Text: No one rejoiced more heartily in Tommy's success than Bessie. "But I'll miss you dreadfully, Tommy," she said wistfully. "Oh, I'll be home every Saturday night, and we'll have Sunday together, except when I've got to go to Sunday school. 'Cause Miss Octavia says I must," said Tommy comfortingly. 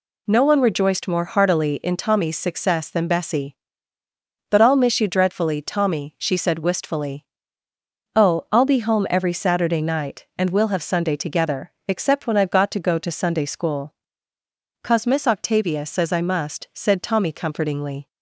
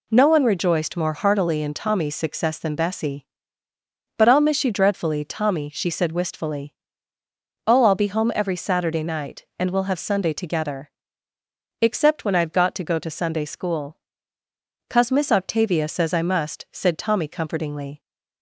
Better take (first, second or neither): neither